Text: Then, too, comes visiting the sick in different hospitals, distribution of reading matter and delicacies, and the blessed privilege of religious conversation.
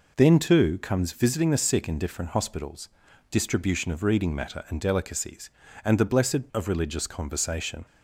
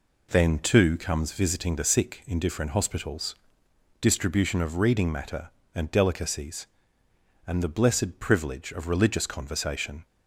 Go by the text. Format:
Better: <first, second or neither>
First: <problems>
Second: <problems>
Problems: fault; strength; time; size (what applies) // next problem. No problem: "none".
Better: second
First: skips "privilege"; at 6.5 s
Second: none